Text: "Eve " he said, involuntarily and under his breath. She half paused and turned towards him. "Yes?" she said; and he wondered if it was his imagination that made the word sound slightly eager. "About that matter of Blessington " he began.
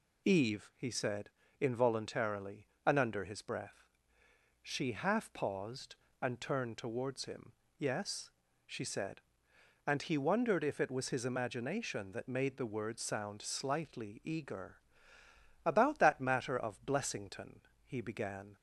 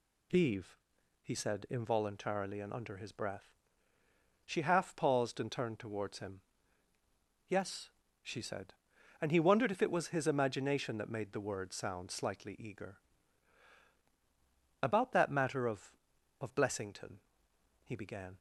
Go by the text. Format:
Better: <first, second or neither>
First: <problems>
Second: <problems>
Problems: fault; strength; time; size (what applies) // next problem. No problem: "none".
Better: first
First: none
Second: says "of" twice; at 16.3 s